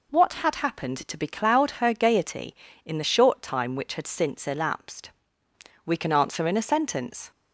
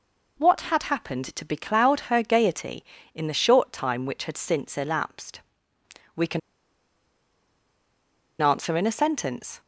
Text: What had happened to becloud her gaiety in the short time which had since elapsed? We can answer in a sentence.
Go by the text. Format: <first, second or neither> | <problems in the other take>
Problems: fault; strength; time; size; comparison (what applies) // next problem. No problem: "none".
first | pauses between "can" and "answer"; strong; at 6.3 s; 2.0 s long